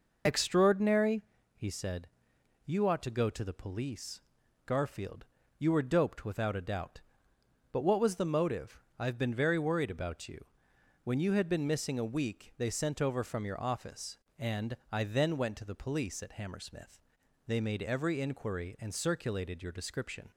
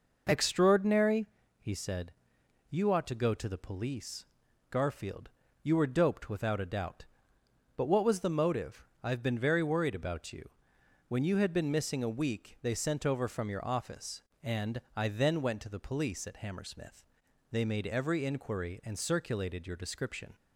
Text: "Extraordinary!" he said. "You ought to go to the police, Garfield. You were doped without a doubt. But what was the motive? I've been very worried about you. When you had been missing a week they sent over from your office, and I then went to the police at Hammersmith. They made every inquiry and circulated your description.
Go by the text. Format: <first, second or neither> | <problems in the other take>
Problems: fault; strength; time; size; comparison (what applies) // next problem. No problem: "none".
second | loses the start of "Extraordinary"; at 0.2 s; 25 ms // pauses between "and" and "I"; slight; at 14.7 s; 0.16 s long; slight in the second